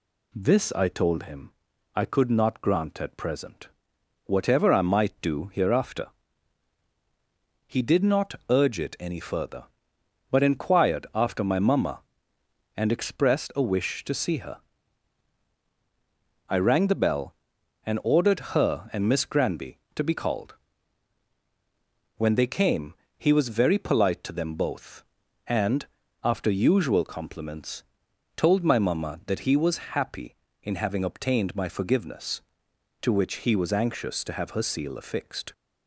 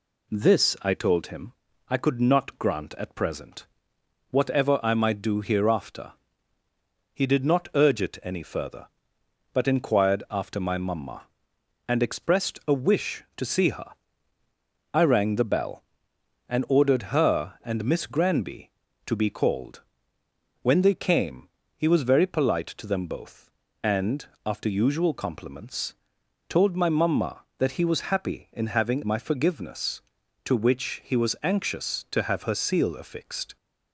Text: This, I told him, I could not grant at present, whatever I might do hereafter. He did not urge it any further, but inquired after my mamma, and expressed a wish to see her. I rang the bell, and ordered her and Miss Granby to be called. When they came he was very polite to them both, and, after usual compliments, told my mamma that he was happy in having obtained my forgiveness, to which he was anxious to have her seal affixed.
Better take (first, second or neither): first